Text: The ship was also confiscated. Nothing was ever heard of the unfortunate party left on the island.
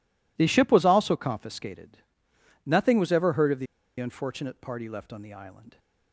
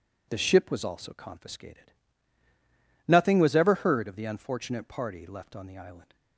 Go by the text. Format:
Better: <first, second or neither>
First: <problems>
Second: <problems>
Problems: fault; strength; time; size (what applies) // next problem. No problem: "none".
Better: second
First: pauses between "the" and "unfortunate"; slight; at 3.6 s; 0.34 s long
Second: none